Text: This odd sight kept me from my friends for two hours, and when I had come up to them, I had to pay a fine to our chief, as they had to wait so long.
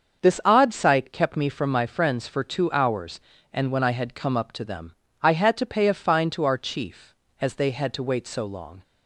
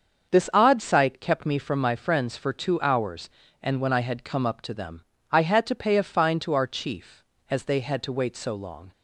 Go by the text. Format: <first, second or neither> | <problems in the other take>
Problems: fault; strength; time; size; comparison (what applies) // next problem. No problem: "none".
neither | starts louder than the rest; the same in both